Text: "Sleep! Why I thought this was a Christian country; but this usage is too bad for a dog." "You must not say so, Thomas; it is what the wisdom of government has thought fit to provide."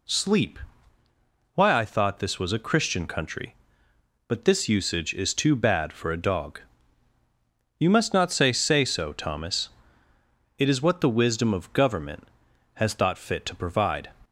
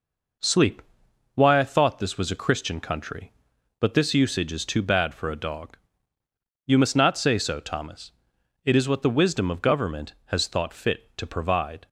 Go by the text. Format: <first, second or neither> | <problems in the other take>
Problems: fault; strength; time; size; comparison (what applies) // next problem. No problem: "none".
second | says "say" twice; at 8.5 s